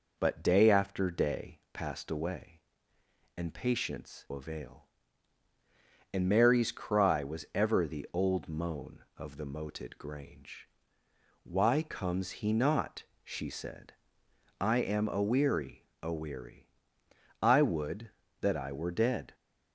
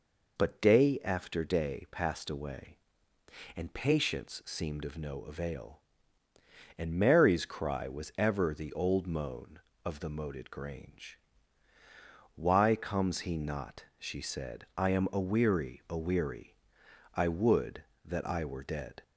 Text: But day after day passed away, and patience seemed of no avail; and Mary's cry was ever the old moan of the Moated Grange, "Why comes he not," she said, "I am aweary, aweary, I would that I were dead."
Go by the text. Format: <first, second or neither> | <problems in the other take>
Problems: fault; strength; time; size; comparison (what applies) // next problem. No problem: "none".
second | skips "seemed of no"; at 4.2 s